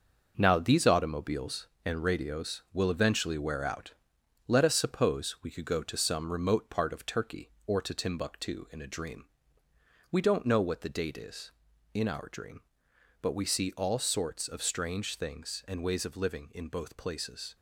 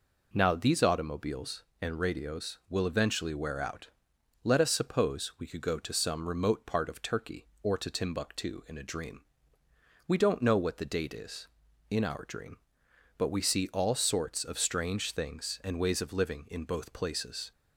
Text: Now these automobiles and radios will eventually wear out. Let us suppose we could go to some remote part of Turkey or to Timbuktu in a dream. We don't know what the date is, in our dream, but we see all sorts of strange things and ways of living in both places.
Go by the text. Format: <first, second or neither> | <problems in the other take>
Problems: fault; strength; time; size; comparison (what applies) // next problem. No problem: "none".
second | gets quieter; throughout; 7 dB